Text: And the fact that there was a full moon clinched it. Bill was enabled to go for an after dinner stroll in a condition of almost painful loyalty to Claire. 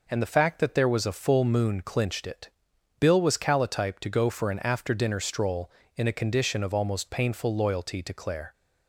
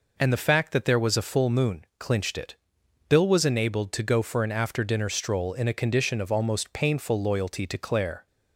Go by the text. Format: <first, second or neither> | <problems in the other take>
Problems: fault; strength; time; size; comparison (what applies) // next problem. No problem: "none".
second | says "calotype" for "enabled"; at 3.3 s